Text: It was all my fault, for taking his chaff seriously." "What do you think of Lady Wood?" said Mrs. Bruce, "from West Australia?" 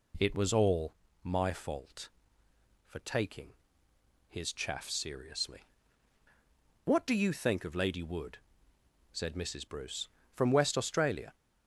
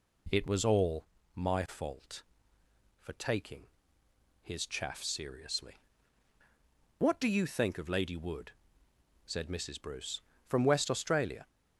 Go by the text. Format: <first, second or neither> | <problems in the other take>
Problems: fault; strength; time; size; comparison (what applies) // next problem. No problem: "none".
neither | pauses between "all" and "my"; slight; the same in both // pauses between "taking" and "his"; noticeable; the same in both